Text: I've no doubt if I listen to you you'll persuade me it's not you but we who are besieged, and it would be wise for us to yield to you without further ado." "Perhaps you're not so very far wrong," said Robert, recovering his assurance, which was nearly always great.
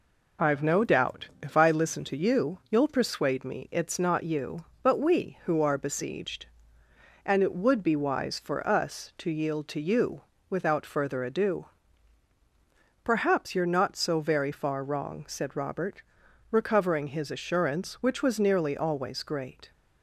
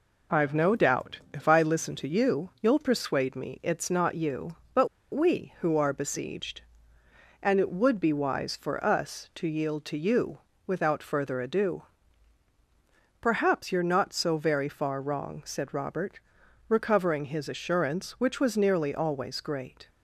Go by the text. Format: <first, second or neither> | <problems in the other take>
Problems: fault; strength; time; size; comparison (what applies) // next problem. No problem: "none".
first | pauses between "but" and "we"; slight; at 4.8 s; 0.25 s long // pauses between "you" and "without"; slight; at 10.3 s; 0.28 s long; slight in the first